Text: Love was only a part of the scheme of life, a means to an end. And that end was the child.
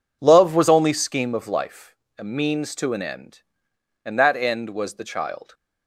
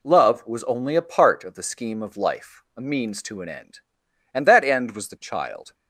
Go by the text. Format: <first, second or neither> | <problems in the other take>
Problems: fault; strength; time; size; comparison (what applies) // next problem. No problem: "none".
second | skips "a part of the"; at 0.9 s